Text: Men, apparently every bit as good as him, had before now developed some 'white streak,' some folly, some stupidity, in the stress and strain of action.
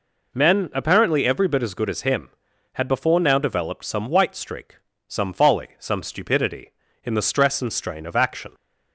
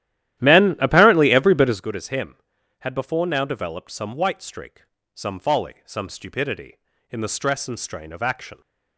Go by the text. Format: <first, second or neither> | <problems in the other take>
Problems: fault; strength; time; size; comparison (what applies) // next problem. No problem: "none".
first | starts louder than the rest; strong; until 1.8 s; 12.5 dB